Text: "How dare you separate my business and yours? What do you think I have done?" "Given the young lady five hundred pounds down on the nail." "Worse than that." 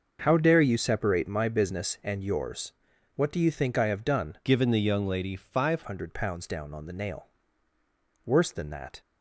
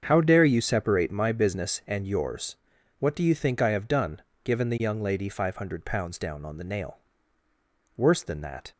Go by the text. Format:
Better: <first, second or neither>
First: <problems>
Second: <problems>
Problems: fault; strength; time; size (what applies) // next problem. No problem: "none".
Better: second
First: starts louder than the rest; noticeable; until 1.2 s; 6 dB // changes voice from "Given" to "five"; from 4.4 to 5.8 s; 1.4 s long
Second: starts louder than the rest; until 1.0 s; 7 dB